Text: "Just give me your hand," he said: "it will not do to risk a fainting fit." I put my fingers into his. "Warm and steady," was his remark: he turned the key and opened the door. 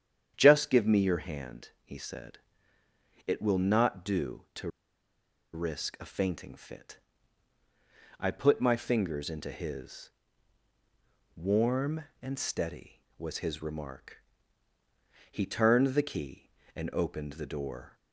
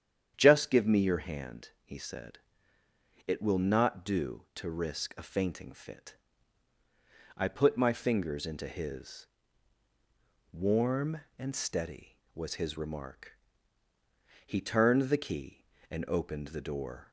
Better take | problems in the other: second | starts louder than the rest; strong; until 1.3 s; 9 dB; strong in the second // pauses between "to" and "risk"; noticeable; at 4.6 s; 0.85 s long

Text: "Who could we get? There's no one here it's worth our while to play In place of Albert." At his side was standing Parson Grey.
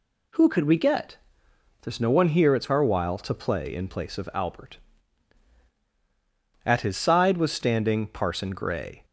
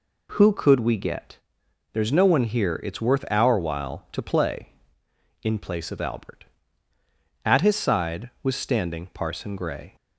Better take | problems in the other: second | skips "worth"; at 2.7 s

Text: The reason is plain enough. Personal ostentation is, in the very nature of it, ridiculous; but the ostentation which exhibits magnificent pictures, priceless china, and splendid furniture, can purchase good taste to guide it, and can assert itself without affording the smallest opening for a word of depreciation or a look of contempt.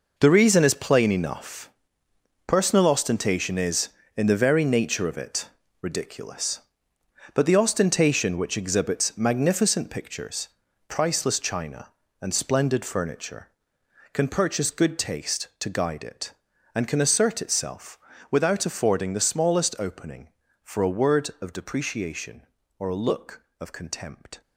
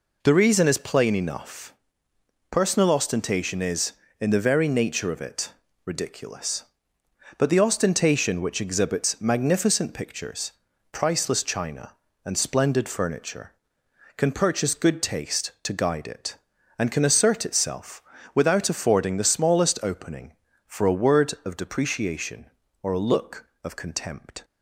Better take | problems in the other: second | gets quieter; strong; throughout; 11.5 dB // pauses between "itself" and "without"; slight; at 17.9 s; 0.32 s long; slight in the second

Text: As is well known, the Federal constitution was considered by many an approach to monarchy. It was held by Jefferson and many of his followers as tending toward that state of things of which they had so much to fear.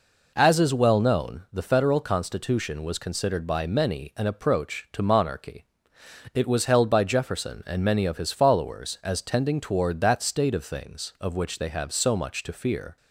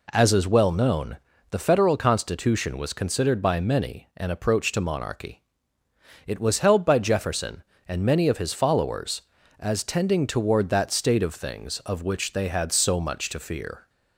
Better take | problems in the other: second | says "have" for "had"; at 11.6 s

